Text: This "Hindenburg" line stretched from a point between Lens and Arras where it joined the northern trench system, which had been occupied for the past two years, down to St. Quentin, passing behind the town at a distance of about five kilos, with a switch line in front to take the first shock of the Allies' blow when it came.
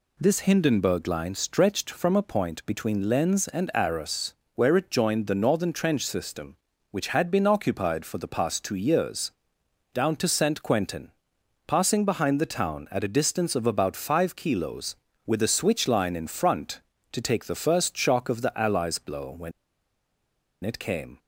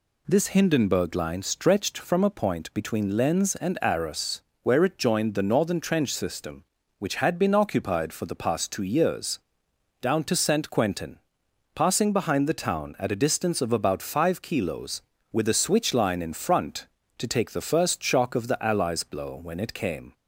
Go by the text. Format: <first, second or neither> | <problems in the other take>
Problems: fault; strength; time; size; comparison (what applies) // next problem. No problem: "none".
second | pauses between "Arras" and "where"; slight; at 4.3 s; 0.22 s long; slight in the second // pauses between "when" and "it"; at 19.5 s; 1.1 s long